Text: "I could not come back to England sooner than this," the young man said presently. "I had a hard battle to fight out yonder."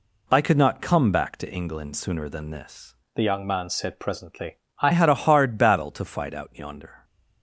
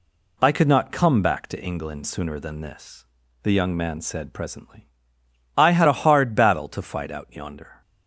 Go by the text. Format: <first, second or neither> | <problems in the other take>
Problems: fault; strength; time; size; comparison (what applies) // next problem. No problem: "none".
second | changes voice from "the" to "I"; from 3.1 to 4.9 s; 1.8 s long